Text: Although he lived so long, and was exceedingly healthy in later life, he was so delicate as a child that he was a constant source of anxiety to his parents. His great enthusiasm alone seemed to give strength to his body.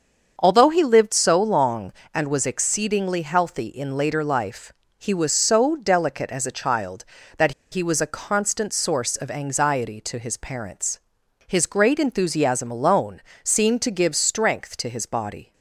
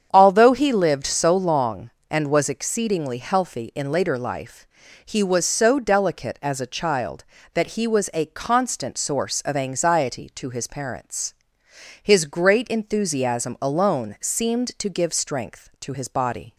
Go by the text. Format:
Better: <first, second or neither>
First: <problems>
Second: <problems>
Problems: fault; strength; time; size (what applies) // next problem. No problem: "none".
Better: second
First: starts louder than the rest; until 1.3 s; 7 dB // pauses between "that" and "he"; slight; at 7.5 s; 0.19 s long // pauses between "alone" and "seemed"; slight; at 13.2 s; 0.22 s long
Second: starts louder than the rest; strong; until 1.1 s; 8 dB